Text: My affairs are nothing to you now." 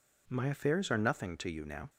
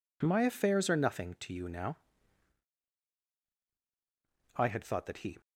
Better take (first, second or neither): first